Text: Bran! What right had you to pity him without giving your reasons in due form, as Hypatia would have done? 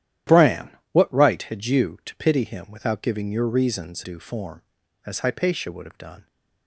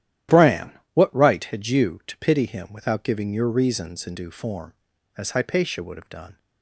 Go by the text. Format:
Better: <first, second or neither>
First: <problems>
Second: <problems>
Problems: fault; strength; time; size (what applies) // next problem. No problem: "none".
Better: second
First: starts louder than the rest; strong; until 1.4 s; 12 dB // skips "in"; at 4.0 s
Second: starts louder than the rest; strong; until 1.5 s; 12.5 dB